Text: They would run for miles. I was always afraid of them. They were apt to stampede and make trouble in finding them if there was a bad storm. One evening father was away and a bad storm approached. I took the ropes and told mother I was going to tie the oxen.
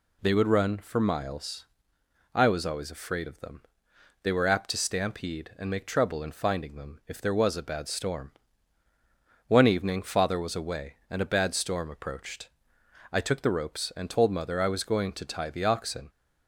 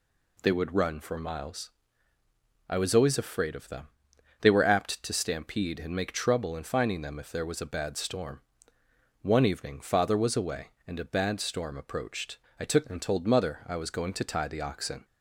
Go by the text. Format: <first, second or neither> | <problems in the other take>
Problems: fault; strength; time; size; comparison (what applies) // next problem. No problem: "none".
first | skips "the ropes"; at 12.8 s